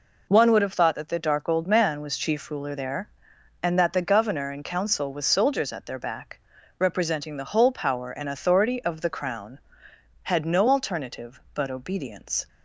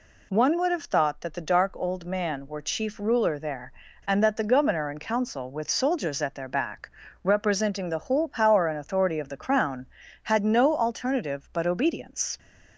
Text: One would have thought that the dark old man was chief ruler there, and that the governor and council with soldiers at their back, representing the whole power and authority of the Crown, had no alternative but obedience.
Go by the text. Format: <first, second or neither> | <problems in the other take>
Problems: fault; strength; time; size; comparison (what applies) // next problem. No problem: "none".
first | says "were" for "was"; at 2.4 s